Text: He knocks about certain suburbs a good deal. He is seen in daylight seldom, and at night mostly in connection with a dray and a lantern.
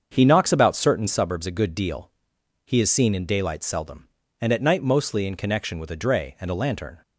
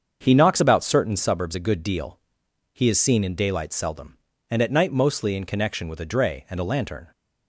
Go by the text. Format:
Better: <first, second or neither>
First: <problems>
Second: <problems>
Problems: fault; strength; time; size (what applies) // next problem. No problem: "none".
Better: neither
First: starts louder than the rest; until 1.1 s; 7 dB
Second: starts louder than the rest; until 1.2 s; 7 dB